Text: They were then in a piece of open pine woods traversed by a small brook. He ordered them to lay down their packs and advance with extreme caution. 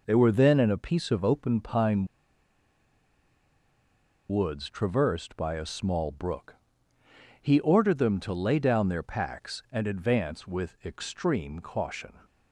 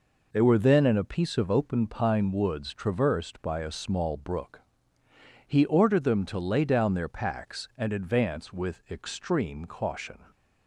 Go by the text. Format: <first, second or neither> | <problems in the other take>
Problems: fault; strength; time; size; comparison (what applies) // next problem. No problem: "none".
second | pauses between "pine" and "woods"; strong; at 2.0 s; 2.2 s long